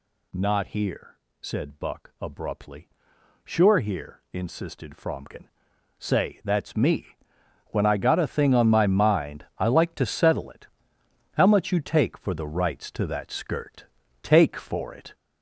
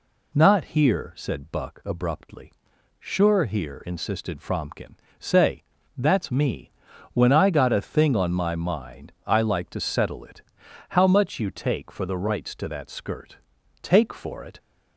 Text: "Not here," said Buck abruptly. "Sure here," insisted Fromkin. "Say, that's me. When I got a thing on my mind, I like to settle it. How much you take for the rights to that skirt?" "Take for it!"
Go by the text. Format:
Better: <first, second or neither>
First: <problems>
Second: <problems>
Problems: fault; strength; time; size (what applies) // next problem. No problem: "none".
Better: second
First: gets louder; noticeable; throughout; 5.5 dB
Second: none